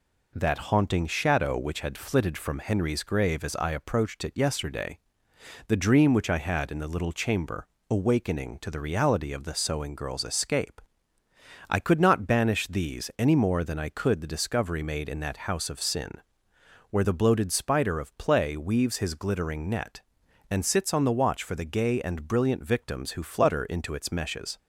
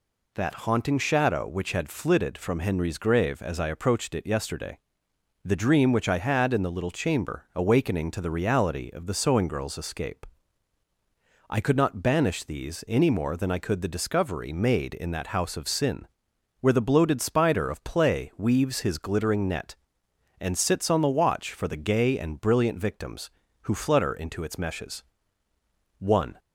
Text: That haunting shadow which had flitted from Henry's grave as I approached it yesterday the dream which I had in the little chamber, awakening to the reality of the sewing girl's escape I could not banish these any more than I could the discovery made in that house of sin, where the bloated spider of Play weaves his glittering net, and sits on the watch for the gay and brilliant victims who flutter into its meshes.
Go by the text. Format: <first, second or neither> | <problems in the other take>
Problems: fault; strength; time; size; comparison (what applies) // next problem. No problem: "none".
first | pauses between "yesterday" and "the"; noticeable; at 4.7 s; 0.64 s long; noticeable in the first // pauses between "escape" and "I"; at 10.2 s; 1.2 s long; noticeable in the first // goes on to say "One"; slight; from 25.9 s on; 0.38 s long